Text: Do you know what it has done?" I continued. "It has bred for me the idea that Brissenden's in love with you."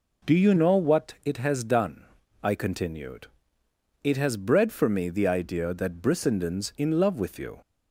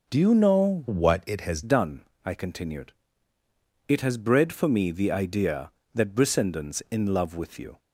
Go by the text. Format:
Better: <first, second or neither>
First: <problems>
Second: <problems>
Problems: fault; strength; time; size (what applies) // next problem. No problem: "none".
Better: first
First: none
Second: changes voice from "what" to "has"; from 0.8 to 1.6 s; 0.8 s long